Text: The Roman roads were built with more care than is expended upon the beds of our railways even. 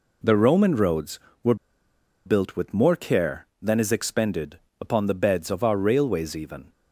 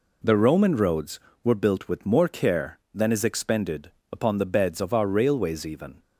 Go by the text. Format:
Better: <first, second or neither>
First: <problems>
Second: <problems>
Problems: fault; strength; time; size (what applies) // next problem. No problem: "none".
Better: second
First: pauses between "were" and "built"; noticeable; at 1.5 s; 0.70 s long // pauses between "expended" and "upon"; slight; at 4.5 s; 0.24 s long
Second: pauses between "expended" and "upon"; slight; at 3.8 s; 0.23 s long